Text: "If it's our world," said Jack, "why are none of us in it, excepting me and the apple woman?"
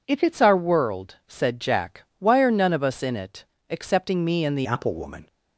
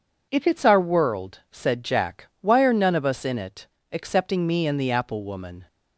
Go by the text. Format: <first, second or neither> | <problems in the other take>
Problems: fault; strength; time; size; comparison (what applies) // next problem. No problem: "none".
second | changes voice at "apple"; from 4.6 s on; 0.6 s long